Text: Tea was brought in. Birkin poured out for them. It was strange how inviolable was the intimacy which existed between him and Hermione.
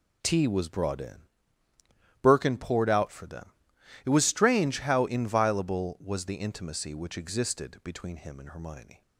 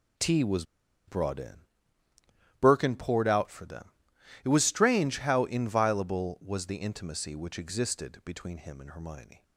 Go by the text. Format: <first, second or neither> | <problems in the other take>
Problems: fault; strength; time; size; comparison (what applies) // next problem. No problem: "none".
first | pauses between "was" and "brought"; at 0.6 s; 0.43 s long